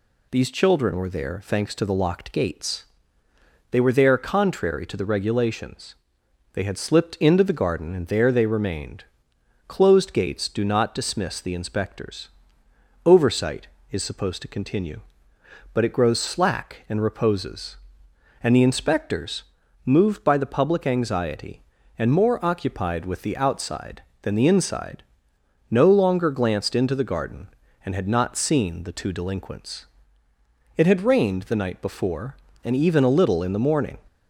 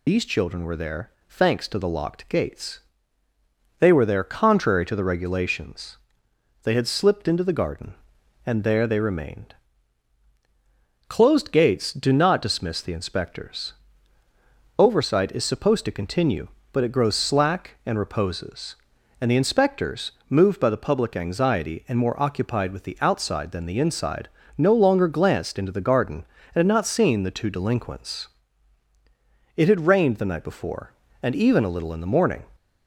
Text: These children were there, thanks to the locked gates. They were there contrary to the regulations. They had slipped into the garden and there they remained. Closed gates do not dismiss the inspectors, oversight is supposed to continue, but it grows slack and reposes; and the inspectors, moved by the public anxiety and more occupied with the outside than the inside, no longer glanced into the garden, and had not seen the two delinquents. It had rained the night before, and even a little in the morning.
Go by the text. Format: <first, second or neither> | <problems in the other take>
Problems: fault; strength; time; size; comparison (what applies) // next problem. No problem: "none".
first | loses the start of "These"; at 0.0 s; 95 ms